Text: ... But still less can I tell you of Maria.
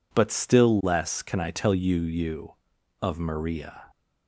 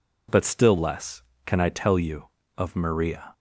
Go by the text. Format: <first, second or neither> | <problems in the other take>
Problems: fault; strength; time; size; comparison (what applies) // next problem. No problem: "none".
second | says "you" twice; at 2.0 s